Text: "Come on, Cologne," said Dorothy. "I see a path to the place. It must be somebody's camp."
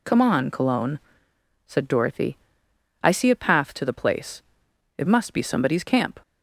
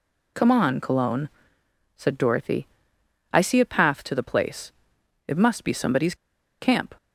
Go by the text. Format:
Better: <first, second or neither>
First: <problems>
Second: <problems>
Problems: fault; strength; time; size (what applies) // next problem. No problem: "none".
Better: first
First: none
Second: pauses between "somebody's" and "camp"; at 6.1 s; 0.44 s long